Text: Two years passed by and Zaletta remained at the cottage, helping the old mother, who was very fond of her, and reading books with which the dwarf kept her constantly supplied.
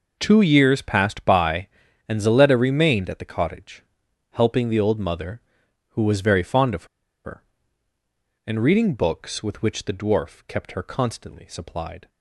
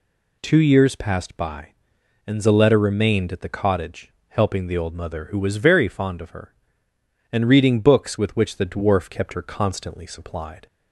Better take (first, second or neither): second